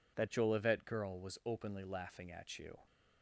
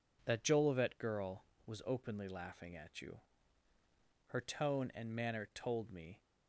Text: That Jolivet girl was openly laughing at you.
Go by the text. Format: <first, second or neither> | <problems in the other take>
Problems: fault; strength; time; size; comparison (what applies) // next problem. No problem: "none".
first | goes on to say "Her tone and manner told me"; strong; from 4.2 s on; 1.9 s long